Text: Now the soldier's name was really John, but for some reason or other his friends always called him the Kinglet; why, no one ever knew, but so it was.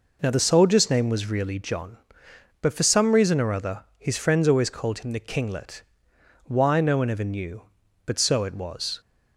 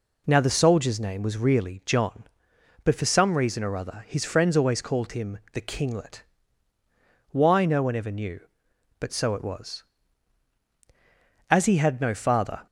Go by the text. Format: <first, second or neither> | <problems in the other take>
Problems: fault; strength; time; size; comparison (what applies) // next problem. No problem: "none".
first | pauses between "him" and "the"; slight; at 5.3 s; 0.16 s long // goes on to say "As he had no father"; noticeable; from 11.4 s on; 1.1 s long